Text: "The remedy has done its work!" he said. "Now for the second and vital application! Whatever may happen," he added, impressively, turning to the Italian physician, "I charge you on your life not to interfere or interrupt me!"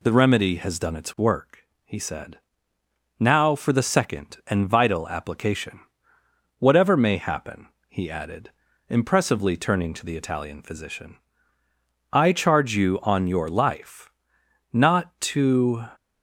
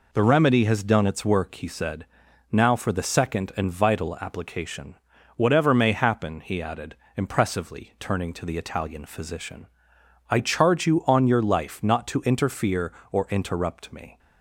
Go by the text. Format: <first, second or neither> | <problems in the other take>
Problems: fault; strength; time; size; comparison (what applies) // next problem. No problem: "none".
second | pauses between "life" and "not"; noticeable; at 14.1 s; 0.60 s long // stops before "interfere or interrupt me"; at 15.9 s